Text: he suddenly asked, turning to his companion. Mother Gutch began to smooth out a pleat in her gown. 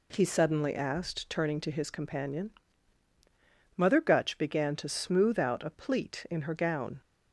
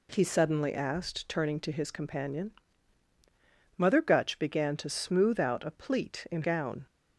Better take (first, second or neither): first